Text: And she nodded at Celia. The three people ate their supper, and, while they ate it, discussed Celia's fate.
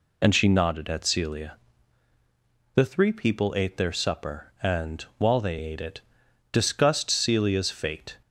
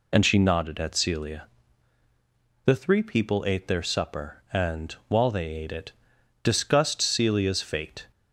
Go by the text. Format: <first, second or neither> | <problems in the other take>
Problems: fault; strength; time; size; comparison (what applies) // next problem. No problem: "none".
neither | none